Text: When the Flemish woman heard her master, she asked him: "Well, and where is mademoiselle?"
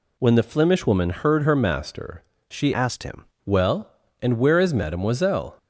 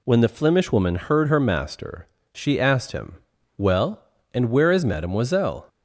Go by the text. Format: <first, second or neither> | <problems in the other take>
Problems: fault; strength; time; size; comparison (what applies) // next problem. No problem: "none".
second | changes voice from "asked" to "him"; from 2.7 to 3.2 s; 0.5 s long